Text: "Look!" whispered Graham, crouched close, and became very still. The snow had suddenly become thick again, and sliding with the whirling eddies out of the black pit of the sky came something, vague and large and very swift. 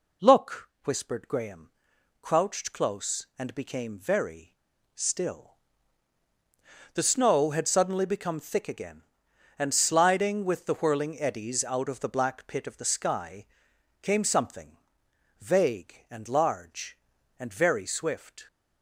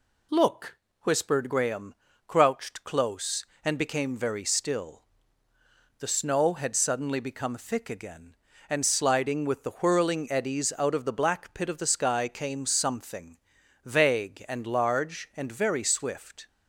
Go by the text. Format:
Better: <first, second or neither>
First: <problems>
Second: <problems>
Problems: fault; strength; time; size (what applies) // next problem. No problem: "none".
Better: second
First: pauses between "very" and "still"; at 4.5 s; 0.39 s long // pauses between "sky" and "came"; noticeable; at 13.4 s; 0.56 s long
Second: none